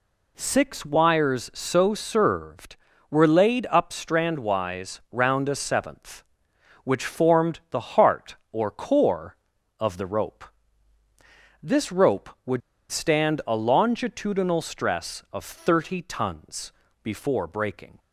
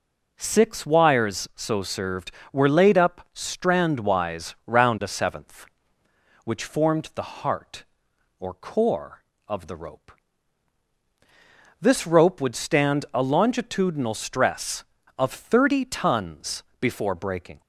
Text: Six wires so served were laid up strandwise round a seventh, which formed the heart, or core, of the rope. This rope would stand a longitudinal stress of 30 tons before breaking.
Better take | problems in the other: second | pauses between "would" and "stand"; slight; at 12.6 s; 0.29 s long // pauses between "tons" and "before"; slight; at 16.7 s; 0.30 s long; slight in the second

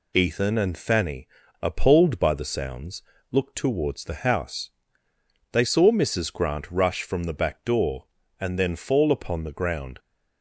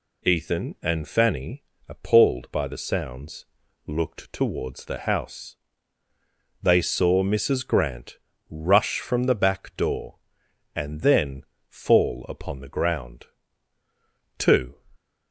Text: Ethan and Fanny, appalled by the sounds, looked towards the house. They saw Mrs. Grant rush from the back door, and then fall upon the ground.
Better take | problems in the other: first | pauses between "Grant" and "rush"; slight; at 8.1 s; 0.30 s long // pauses between "then" and "fall"; slight; at 11.4 s; 0.24 s long // goes on to say "Two"; slight; from 14.3 s on; 0.44 s long

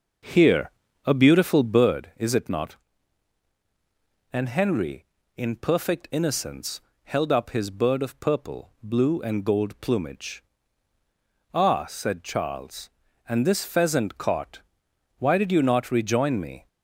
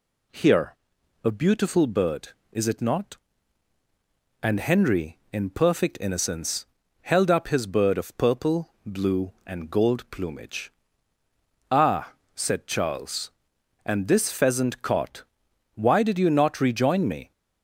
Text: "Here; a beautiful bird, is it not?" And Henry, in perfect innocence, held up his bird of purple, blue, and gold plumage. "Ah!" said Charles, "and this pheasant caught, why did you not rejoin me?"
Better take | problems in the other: second | starts louder than the rest; noticeable; until 2.1 s; 6 dB

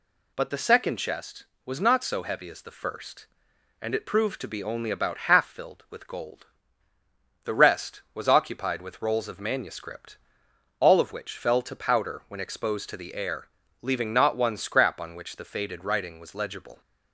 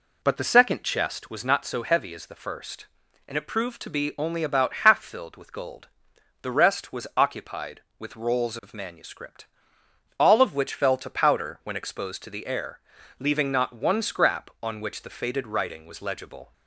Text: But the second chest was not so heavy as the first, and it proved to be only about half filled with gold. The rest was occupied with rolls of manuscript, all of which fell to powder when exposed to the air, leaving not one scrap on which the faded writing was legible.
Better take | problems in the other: first | starts louder than the rest; slight; until 1.4 s; 3.5 dB

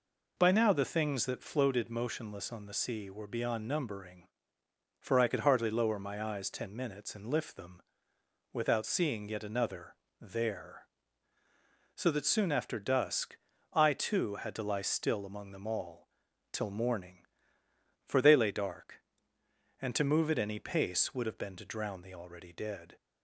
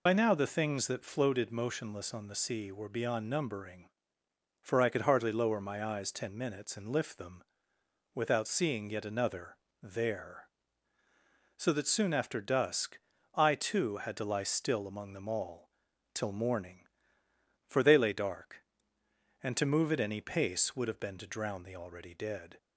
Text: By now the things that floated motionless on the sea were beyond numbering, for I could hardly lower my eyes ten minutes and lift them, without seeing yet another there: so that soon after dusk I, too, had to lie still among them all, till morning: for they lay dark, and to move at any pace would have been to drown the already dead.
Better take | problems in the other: first | loses the start of "By"; at 0.0 s; 60 ms // pauses between "another" and "there"; slight; at 9.5 s; 0.24 s long; slight in the first // pauses between "dusk" and "I"; slight; at 12.9 s; 0.36 s long; slight in the first

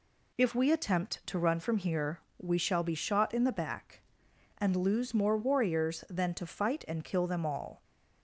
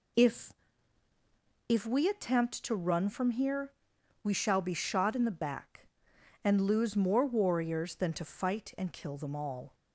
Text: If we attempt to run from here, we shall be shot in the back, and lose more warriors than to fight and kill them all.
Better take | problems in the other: first | says "If" twice; at 1.6 s

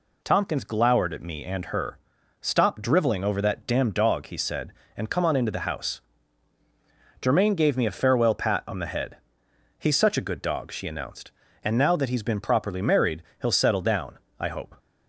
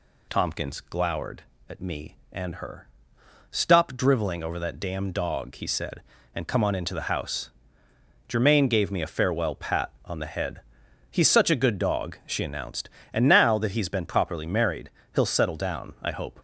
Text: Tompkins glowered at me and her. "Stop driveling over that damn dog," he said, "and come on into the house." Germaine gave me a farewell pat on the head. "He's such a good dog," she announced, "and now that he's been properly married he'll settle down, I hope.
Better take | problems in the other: neither | pauses between "married" and "he'll"; slight; the same in both

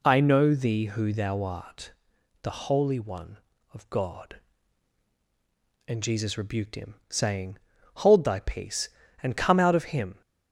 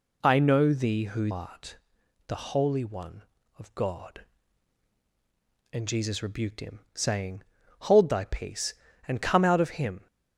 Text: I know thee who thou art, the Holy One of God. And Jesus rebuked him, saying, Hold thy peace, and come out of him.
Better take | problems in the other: first | skips "thou"; at 1.3 s

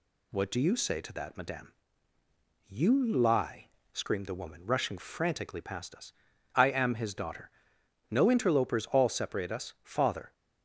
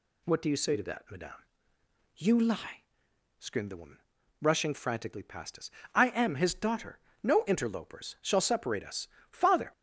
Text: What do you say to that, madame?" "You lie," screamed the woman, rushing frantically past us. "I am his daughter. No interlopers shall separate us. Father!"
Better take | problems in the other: second | says "all" for "shall"; at 8.9 s

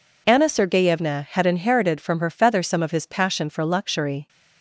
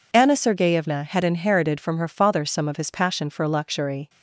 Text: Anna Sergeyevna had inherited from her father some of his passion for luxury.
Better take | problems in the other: second | says "feather" for "father"; at 2.2 s

